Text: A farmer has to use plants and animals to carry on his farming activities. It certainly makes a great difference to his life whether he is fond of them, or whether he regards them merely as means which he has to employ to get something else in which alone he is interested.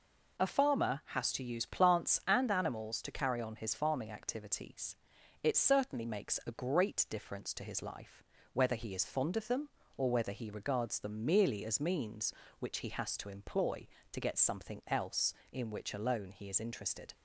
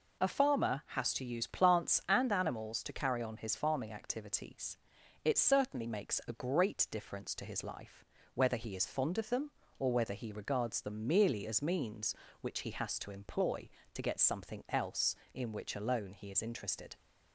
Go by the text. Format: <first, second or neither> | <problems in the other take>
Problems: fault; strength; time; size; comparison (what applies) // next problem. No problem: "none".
neither | pauses between "life" and "whether"; slight; the same in both